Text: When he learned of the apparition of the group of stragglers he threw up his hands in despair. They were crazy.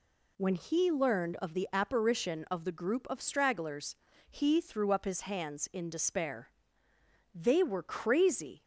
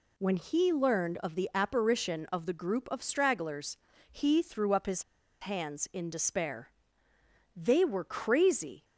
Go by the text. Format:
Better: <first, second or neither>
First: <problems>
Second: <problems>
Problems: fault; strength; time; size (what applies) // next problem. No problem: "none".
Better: first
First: pauses between "stragglers" and "he"; slight; at 3.9 s; 0.36 s long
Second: pauses between "stragglers" and "he"; slight; at 3.7 s; 0.36 s long // pauses between "his" and "hands"; at 5.0 s; 0.38 s long